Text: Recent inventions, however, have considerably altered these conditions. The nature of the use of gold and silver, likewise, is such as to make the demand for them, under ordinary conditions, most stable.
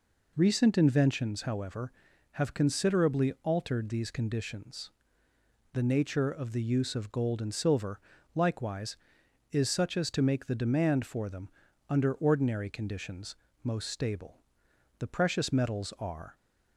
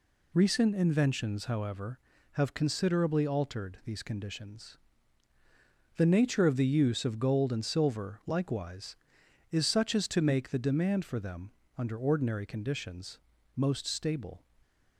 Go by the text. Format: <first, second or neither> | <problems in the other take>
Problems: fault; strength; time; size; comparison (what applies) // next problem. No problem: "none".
second | goes on to say "The precious metals are"; from 14.9 s on; 1.3 s long